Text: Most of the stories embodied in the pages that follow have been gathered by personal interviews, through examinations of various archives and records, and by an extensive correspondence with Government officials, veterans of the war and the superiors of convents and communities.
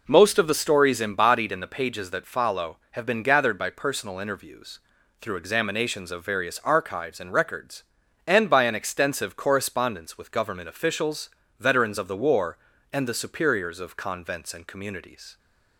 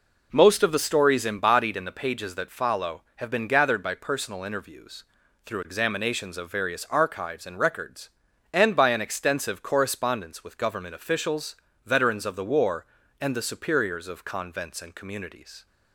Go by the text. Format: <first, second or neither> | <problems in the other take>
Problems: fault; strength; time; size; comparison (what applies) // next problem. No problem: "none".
neither | none